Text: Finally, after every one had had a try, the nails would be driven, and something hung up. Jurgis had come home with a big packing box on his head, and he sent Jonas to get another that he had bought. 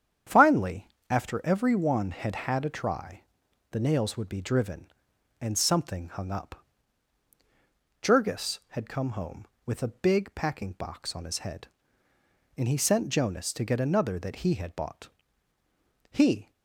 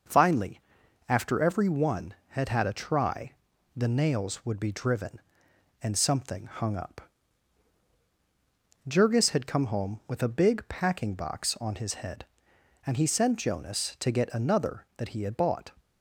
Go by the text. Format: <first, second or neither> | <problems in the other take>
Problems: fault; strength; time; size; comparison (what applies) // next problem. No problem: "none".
second | starts louder than the rest; strong; until 1.5 s; 9 dB // goes on to say "He"; slight; from 16.1 s on; 0.38 s long